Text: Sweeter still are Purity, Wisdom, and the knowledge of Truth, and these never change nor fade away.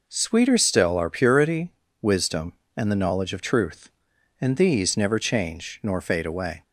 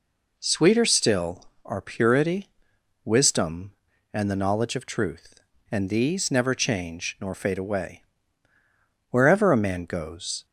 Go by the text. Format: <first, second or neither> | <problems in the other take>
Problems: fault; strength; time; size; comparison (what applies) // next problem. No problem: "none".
first | goes on to say "Wherever a man goes"; from 9.0 s on; 1.3 s long